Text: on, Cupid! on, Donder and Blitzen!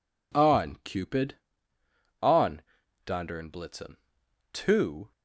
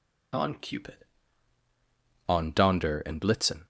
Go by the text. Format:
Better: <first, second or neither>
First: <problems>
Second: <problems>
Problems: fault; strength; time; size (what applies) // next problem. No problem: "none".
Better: second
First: goes on to say "To"; from 4.5 s on; 0.58 s long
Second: none